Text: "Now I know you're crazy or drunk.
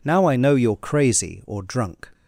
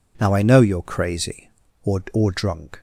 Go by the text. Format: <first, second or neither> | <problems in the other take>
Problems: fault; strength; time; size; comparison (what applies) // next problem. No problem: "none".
first | says "or" twice; at 2.1 s